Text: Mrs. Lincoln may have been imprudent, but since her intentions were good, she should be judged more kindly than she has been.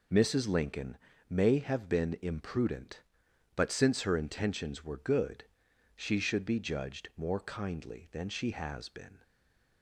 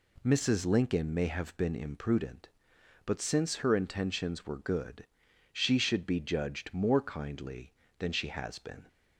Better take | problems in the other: second | pauses between "Lincoln" and "may"; slight; at 0.9 s; 0.34 s long // stays silent after the last word; slight; from 9.2 s on; 0.6 s long

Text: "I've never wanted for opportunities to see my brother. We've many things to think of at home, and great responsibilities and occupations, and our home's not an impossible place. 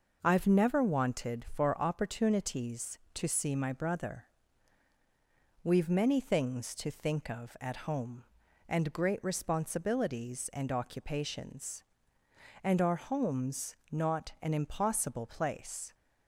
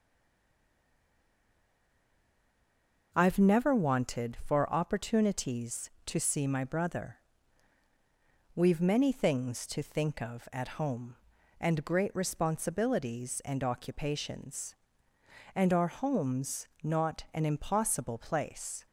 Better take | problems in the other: first | stays silent before the first word; strong; until 3.1 s; 3.1 s long

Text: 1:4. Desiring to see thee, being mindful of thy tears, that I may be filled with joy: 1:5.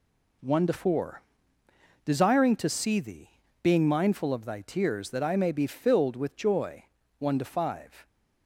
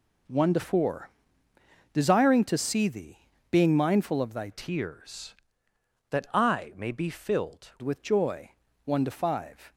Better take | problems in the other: first | changes voice from "tears" to "filled"; from 4.5 to 7.7 s; 3.2 s long

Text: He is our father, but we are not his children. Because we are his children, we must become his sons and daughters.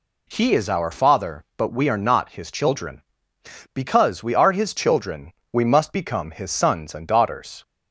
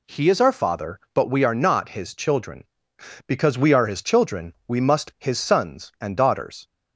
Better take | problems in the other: first | skips "become"; at 5.1 s

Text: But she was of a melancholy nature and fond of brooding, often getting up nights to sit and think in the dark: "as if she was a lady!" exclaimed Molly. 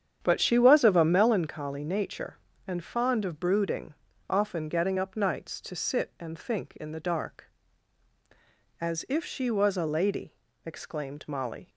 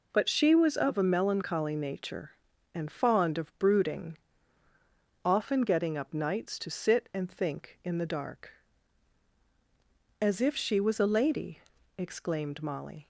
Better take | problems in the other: second | starts louder than the rest; strong; until 1.4 s; 8.5 dB

